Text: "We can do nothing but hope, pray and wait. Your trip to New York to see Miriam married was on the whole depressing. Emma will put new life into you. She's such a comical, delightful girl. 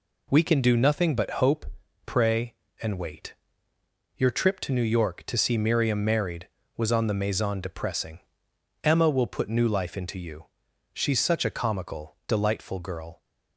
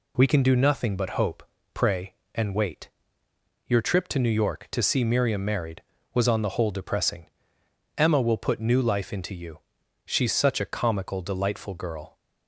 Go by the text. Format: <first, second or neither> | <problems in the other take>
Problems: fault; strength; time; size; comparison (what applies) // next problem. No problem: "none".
second | says "maison" for "whole"; at 7.1 s